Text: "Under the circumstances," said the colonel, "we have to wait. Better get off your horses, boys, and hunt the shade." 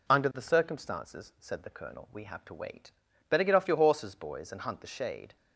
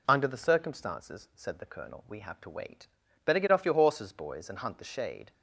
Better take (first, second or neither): neither